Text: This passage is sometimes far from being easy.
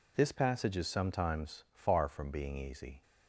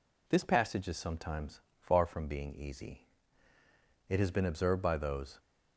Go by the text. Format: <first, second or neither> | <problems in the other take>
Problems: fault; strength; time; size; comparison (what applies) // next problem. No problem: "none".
first | pauses between "sometimes" and "far"; slight; at 1.6 s; 0.18 s long // goes on to say "It has been observed by those"; noticeable; from 4.0 s on; 1.3 s long